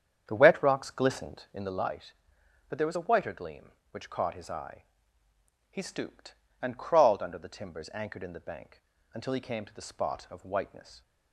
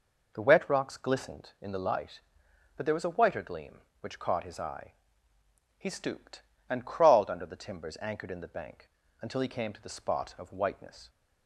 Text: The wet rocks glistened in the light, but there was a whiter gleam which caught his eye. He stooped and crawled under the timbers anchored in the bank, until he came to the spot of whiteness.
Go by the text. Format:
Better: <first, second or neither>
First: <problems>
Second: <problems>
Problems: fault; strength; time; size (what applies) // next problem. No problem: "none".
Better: second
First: starts louder than the rest; strong; until 1.7 s; 8 dB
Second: none